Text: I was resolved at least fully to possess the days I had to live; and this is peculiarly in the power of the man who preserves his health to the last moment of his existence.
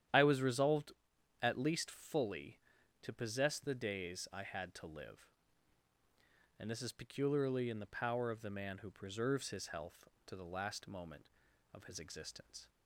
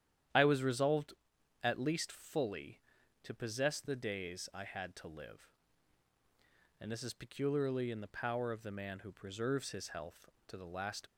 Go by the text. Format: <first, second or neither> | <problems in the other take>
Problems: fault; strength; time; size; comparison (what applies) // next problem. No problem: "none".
first | starts louder than the rest; strong; until 1.8 s; 10 dB; strong in the first // stops before "moment of his existence"; at 11.0 s